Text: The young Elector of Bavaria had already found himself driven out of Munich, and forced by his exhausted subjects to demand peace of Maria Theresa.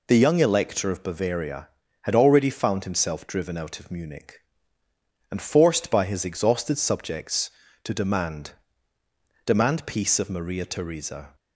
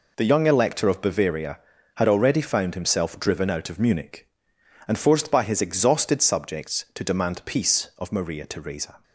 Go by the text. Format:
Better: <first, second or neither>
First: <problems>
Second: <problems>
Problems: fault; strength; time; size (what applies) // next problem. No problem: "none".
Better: second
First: says "demand" twice; at 9.4 s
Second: none